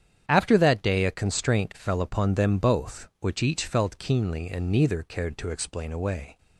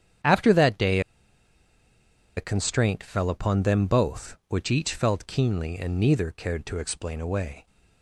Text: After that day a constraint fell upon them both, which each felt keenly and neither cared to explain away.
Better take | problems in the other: first | starts louder than the rest; strong; until 2.6 s; 9 dB; strong in the first // pauses between "day" and "a"; strong; at 0.9 s; 1.3 s long

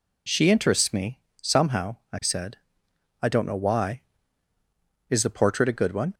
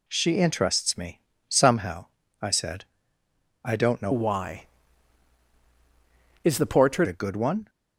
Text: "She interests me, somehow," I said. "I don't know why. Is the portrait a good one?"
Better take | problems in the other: first | changes voice from "why" to "portrait"; from 4.1 to 7.0 s; 2.9 s long

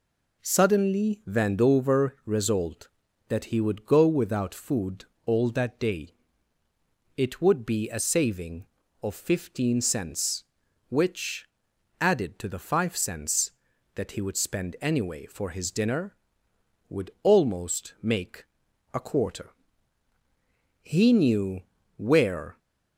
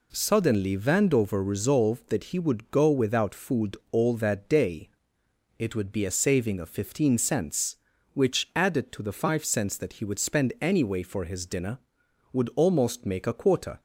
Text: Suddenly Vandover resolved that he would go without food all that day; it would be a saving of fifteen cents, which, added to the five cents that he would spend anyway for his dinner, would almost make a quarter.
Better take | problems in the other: second | pauses between "food" and "all"; slight; at 5.0 s; 0.22 s long; slight in the second // pauses between "make" and "a"; noticeable; at 18.4 s; 0.48 s long // goes on to say "He knew where"; strong; from 20.8 s on; 1.7 s long

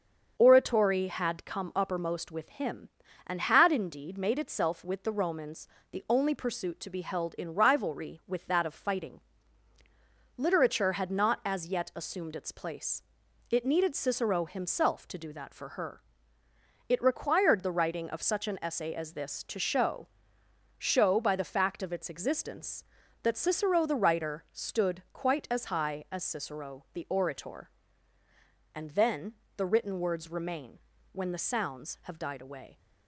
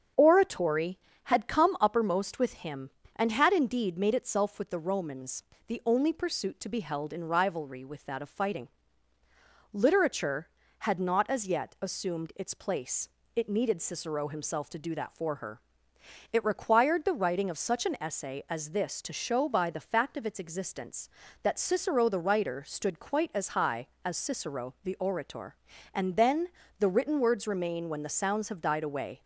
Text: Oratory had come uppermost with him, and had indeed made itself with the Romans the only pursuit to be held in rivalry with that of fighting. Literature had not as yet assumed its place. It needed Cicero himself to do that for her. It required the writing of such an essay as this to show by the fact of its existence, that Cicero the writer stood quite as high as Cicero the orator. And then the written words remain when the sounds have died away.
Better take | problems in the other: second | starts louder than the rest; until 1.3 s; 7 dB; strong in the second // pauses between "Romans" and "the"; slight; at 5.6 s; 0.24 s long; slight in the second // says "show" twice; at 20.7 s // pauses between "then" and "the"; slight; at 29.3 s; 0.24 s long; slight in the second // pauses between "remain" and "when"; slight; at 30.7 s; 0.36 s long

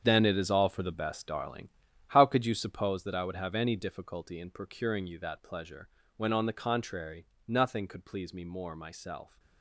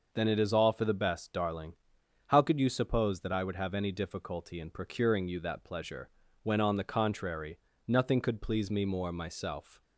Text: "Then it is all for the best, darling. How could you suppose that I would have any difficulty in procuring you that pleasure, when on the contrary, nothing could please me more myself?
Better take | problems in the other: second | gets quieter; strong; throughout; 11.5 dB

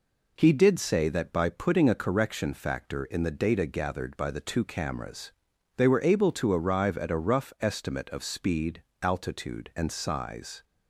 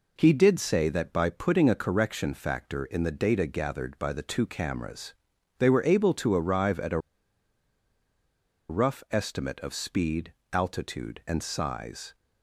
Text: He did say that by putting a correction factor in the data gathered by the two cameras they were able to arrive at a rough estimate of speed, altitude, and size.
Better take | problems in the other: first | pauses between "cameras" and "they"; noticeable; at 5.1 s; 0.46 s long; noticeable in the first // pauses between "a" and "rough"; strong; at 6.9 s; 1.7 s long

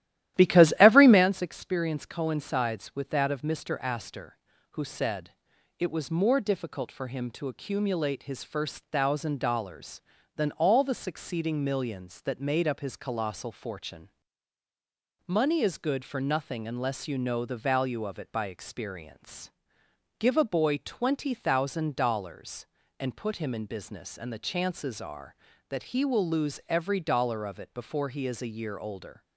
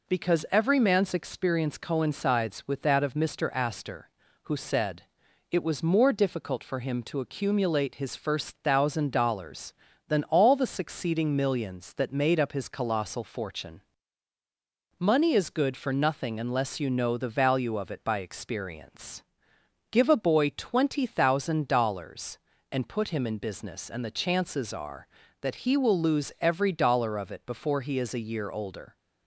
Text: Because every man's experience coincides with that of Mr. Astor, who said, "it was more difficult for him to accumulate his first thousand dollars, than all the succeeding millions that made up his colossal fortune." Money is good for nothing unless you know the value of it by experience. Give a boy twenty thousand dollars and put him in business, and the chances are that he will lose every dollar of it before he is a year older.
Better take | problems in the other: second | starts louder than the rest; strong; until 1.3 s; 13.5 dB

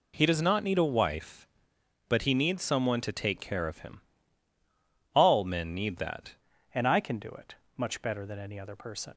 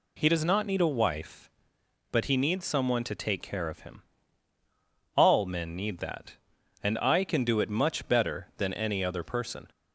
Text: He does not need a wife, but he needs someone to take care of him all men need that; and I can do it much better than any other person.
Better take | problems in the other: second | pauses between "him" and "all"; at 4.0 s; 1.1 s long; also in the second // changes voice at "and"; from 6.7 s on; 2.4 s long // pauses between "it" and "much"; slight; at 7.5 s; 0.22 s long

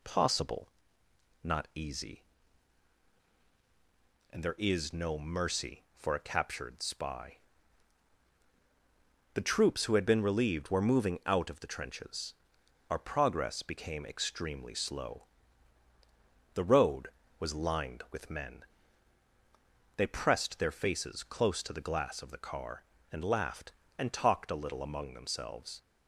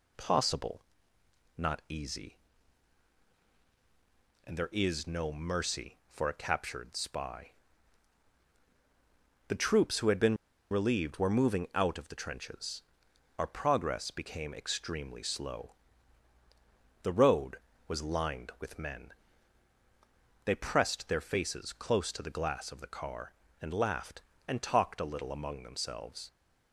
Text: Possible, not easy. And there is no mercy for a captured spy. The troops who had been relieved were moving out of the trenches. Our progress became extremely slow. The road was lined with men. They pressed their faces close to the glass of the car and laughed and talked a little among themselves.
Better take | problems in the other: first | pauses between "been" and "relieved"; slight; at 10.3 s; 0.34 s long

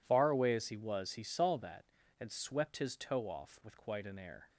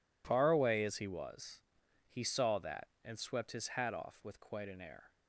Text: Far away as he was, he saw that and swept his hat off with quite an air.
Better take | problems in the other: second | says "toe" for "hat"; at 2.9 s

